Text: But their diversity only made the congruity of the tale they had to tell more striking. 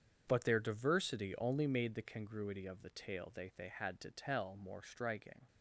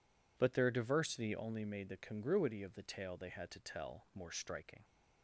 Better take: second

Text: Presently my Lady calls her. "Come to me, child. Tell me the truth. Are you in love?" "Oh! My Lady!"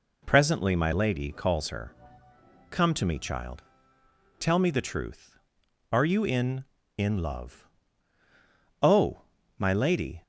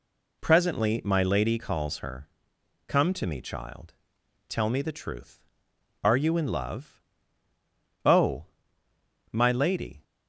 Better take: second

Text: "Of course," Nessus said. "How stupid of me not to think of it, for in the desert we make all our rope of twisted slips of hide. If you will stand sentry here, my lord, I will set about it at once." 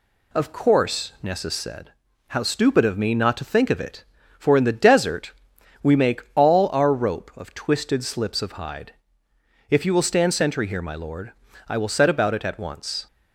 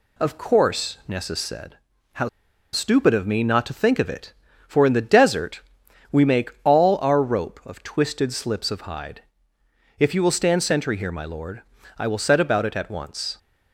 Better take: first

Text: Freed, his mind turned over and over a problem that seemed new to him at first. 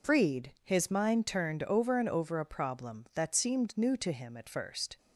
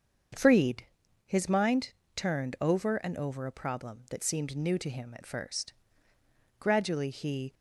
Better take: first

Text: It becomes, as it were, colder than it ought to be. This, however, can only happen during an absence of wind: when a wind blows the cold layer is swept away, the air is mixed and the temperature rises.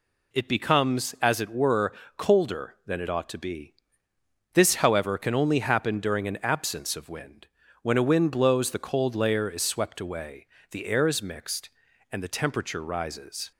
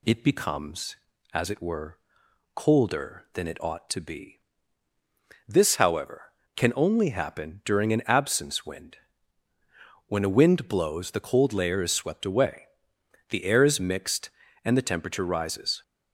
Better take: first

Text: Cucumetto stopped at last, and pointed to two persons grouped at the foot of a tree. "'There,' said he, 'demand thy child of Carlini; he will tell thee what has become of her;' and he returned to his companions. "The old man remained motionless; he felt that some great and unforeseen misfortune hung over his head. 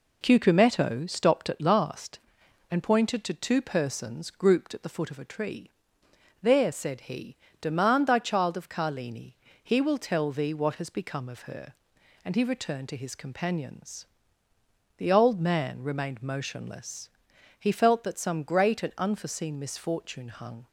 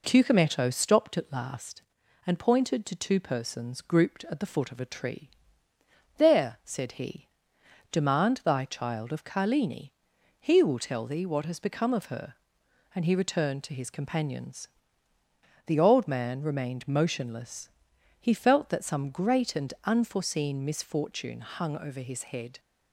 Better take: second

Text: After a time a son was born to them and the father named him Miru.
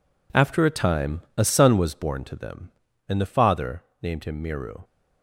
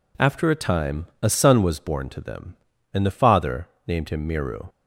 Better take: second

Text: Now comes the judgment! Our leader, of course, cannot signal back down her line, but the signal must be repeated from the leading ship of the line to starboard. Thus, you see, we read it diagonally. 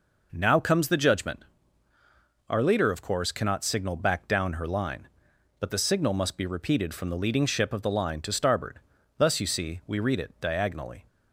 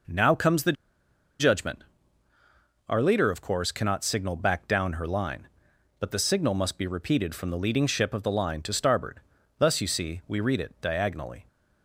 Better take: first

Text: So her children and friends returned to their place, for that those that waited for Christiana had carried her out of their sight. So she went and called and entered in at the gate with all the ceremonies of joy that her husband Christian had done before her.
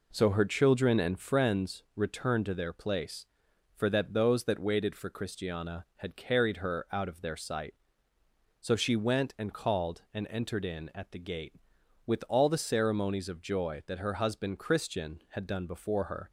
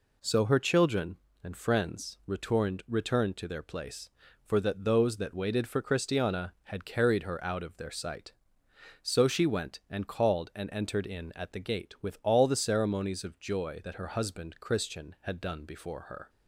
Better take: first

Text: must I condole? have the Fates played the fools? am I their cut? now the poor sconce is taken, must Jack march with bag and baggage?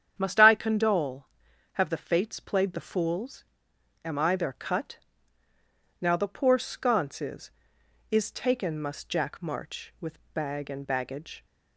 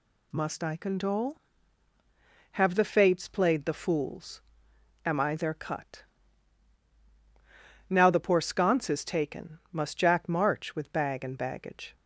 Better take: second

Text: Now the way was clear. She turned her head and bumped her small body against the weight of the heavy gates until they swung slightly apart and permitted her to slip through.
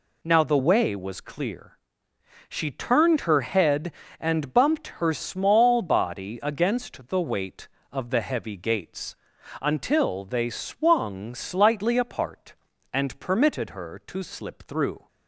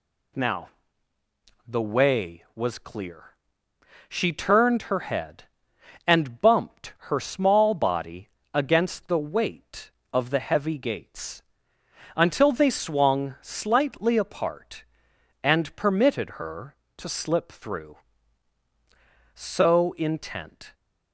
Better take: first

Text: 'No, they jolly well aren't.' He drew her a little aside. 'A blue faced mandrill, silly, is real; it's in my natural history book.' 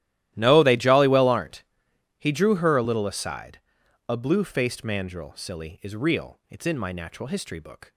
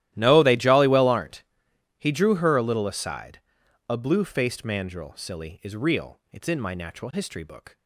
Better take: neither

